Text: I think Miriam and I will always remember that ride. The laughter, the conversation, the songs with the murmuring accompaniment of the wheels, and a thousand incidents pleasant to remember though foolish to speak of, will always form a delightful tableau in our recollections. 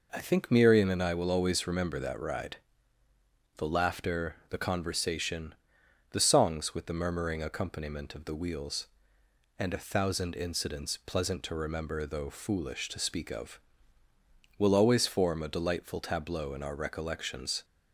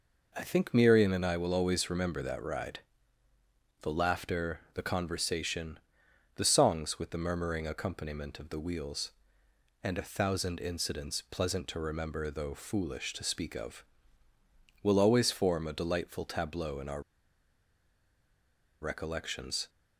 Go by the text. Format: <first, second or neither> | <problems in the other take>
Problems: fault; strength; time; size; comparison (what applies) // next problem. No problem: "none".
first | pauses between "our" and "recollections"; strong; at 17.0 s; 1.7 s long